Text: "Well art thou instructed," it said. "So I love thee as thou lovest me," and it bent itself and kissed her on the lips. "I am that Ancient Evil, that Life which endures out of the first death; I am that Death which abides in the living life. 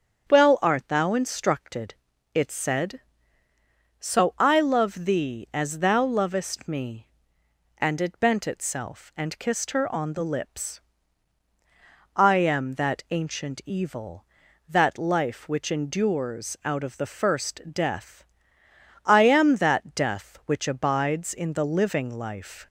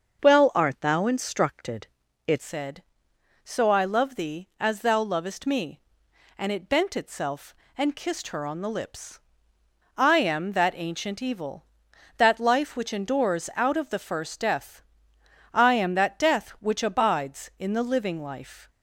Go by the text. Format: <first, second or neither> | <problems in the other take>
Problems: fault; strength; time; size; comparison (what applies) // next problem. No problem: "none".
first | starts louder than the rest; noticeable; until 1.2 s; 6 dB; strong in the first // changes voice at "said"; from 2.4 s on; 16.2 s long